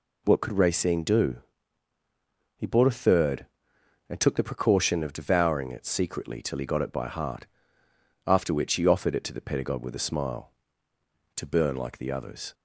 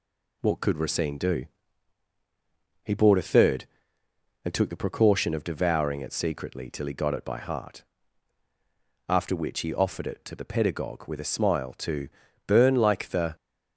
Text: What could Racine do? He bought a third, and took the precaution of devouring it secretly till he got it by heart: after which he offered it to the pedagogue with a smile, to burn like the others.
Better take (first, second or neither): first